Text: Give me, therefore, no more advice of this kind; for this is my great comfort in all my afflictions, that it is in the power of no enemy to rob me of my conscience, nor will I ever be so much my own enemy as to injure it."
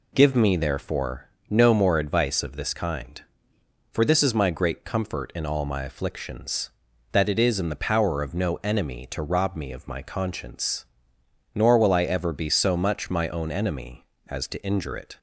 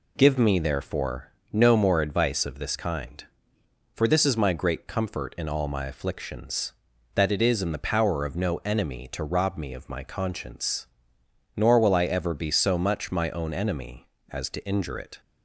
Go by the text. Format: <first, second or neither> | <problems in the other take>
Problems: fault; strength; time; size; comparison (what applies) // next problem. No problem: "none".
neither | none